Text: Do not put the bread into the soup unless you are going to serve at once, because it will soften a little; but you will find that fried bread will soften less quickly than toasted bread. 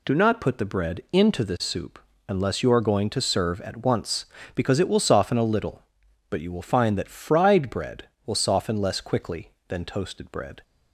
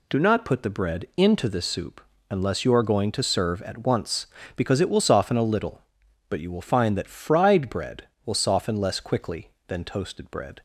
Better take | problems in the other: neither | pauses between "soup" and "unless"; slight; the same in both

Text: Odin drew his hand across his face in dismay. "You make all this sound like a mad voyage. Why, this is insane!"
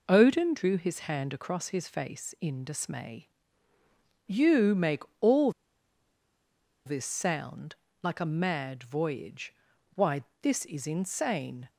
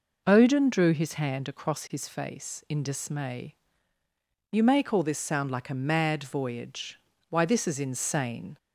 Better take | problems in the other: second | pauses between "make" and "all"; slight; at 5.0 s; 0.20 s long // pauses between "all" and "this"; strong; at 5.4 s; 1.3 s long // pauses between "sound" and "like"; slight; at 7.7 s; 0.26 s long

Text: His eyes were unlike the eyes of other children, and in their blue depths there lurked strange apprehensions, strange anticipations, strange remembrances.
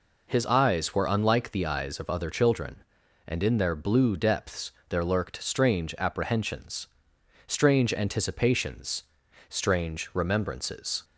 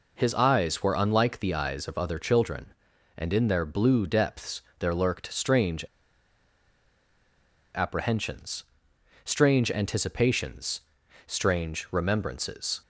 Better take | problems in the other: first | pauses between "depths" and "there"; slight; at 4.6 s; 0.16 s long; slight in the first // pauses between "strange" and "apprehensions"; strong; at 5.8 s; 1.8 s long

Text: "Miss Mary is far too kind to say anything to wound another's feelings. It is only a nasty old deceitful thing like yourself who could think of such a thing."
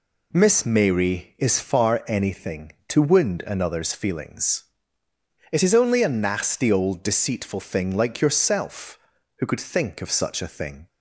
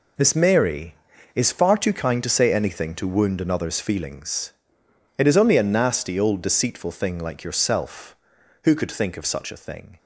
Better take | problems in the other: second | skips "too kind to say"; at 2.0 s

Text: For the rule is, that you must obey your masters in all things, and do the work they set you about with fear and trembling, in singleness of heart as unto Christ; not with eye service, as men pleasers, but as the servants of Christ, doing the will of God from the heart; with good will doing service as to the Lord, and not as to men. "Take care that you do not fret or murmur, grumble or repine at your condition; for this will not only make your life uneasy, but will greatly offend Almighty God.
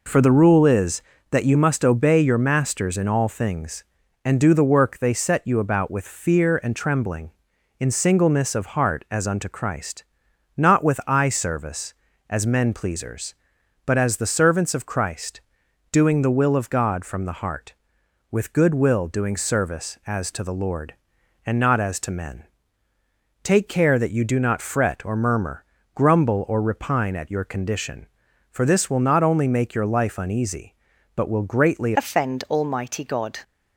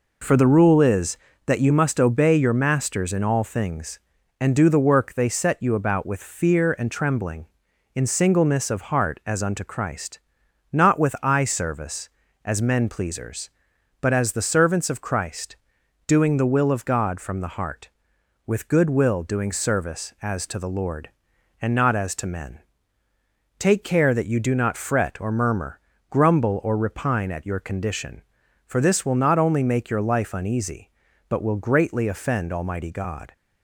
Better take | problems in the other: second | changes voice at "offend"; from 31.9 s on; 1.4 s long

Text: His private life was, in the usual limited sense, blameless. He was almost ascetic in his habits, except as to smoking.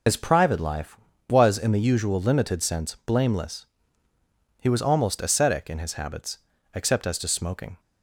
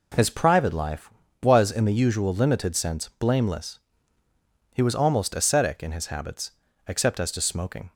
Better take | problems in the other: second | loses the start of "His"; at 0.0 s; 80 ms

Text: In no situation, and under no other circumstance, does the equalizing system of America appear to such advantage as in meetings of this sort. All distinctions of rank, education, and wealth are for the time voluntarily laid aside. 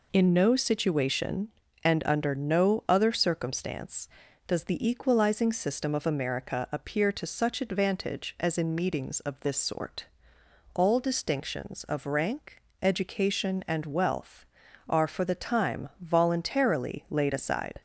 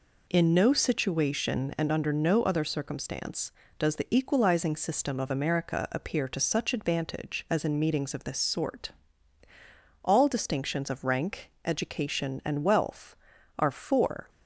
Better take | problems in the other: first | stops before "the time voluntarily laid aside"; at 14.2 s

